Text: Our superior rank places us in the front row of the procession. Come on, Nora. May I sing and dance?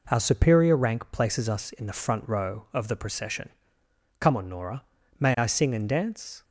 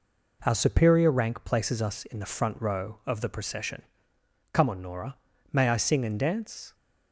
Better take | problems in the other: neither | none

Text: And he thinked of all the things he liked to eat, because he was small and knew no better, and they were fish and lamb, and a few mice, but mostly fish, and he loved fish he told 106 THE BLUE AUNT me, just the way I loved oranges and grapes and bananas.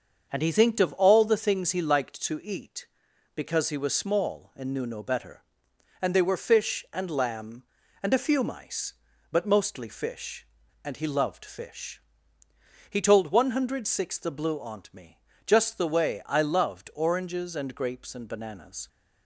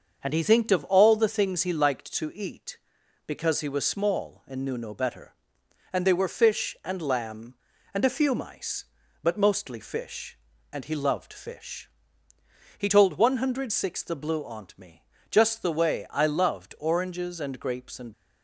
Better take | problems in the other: first | starts louder than the rest; until 1.2 s; 6.5 dB; also in the first // pauses between "fish" and "he"; noticeable; at 11.8 s; 0.90 s long; noticeable in the first // stops before "bananas"; at 18.1 s

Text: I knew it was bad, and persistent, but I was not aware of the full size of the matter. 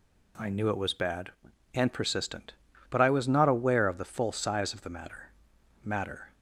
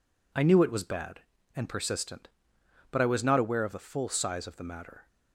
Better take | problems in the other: second | says "matter" twice; at 5.8 s

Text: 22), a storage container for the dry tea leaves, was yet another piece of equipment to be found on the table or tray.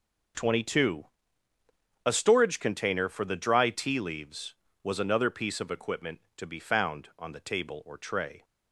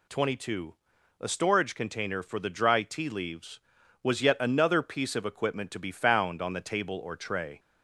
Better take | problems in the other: second | skips "yet"; at 4.9 s

